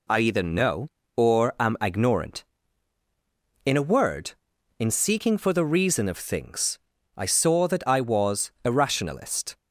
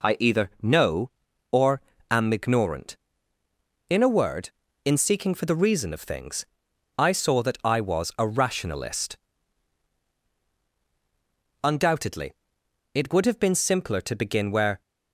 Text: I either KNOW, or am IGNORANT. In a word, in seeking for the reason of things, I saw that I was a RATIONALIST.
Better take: first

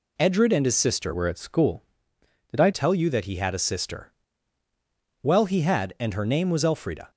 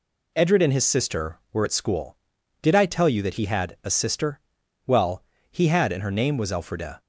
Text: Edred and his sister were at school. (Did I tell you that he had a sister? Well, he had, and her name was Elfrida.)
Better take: second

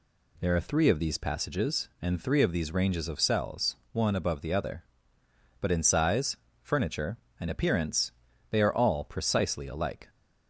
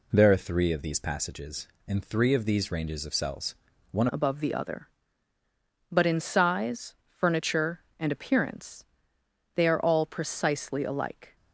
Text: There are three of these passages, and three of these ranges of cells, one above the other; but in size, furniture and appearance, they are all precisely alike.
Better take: first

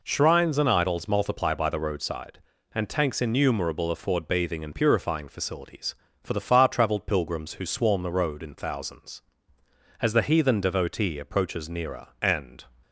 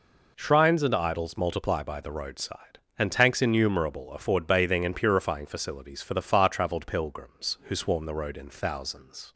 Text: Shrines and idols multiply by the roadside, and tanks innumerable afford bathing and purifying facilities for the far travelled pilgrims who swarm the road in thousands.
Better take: second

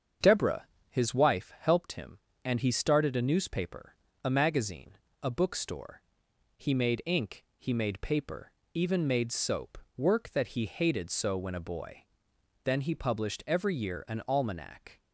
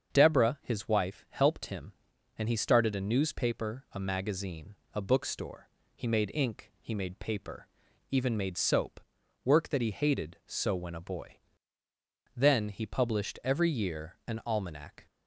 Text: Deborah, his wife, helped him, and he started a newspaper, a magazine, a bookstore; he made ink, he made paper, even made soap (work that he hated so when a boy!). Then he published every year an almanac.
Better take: neither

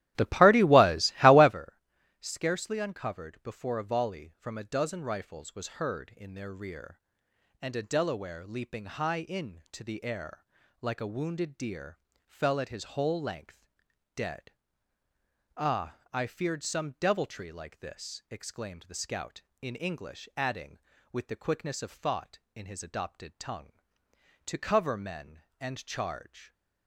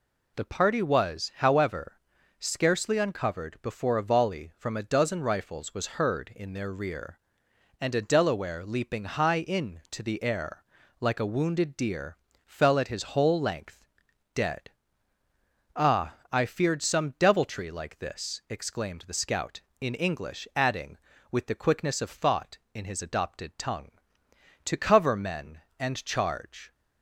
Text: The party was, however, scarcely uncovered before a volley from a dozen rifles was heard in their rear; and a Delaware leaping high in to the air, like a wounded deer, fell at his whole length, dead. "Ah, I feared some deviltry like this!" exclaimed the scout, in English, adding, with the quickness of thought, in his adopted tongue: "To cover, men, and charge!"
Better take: second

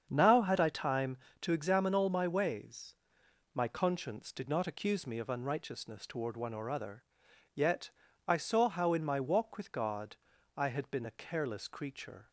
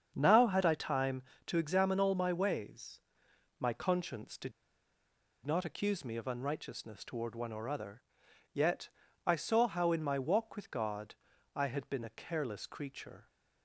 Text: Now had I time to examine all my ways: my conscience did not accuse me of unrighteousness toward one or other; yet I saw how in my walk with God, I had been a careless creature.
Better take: first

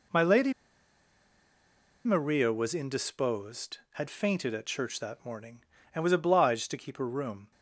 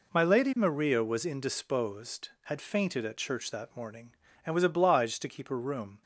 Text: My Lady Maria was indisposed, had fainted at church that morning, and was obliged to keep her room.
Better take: second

